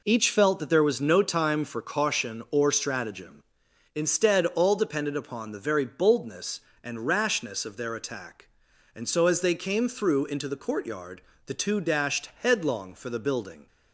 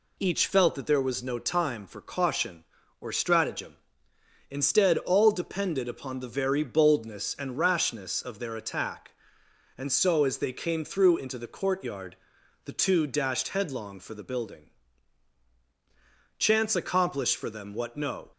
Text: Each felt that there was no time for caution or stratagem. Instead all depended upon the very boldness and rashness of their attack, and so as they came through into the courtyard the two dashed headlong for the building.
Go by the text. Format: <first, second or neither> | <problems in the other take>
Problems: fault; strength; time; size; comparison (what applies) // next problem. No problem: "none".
first | pauses between "courtyard" and "the"; noticeable; at 12.1 s; 0.48 s long; slight in the first // goes on to say "Chance accomplished for them what no"; strong; from 16.3 s on; 1.9 s long